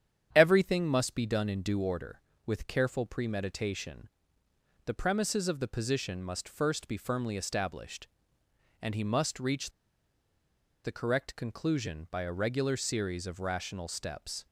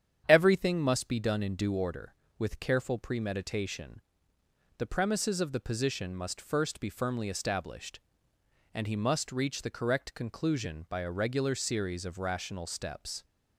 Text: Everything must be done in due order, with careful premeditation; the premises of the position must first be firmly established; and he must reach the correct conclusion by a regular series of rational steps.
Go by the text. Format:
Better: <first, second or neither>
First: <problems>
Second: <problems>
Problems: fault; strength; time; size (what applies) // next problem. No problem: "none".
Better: second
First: starts louder than the rest; strong; until 1.3 s; 8.5 dB // pauses between "reach" and "the"; at 9.7 s; 1.1 s long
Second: starts louder than the rest; strong; until 1.2 s; 8.5 dB